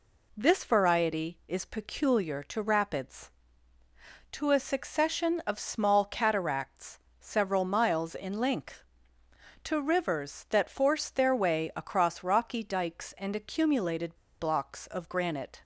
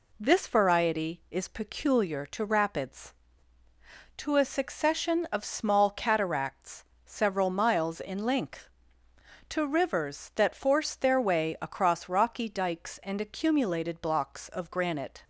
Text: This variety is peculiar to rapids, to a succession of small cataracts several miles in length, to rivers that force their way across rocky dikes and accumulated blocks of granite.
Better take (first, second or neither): second